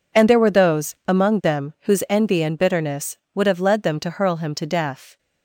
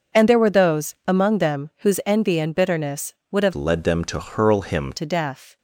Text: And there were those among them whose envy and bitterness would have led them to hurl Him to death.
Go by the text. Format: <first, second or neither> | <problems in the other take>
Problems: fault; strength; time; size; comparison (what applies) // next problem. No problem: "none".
first | changes voice from "led" to "Him"; from 3.5 to 4.9 s; 1.4 s long